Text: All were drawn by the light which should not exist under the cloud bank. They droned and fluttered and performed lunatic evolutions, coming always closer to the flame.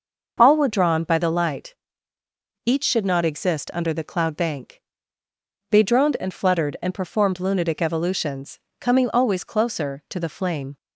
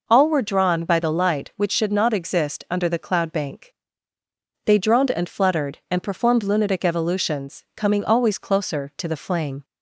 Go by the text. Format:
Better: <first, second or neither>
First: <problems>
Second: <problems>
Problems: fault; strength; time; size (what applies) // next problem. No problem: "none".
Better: second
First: starts louder than the rest; noticeable; until 1.3 s; 6 dB // says "each" for "which"; at 2.6 s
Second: none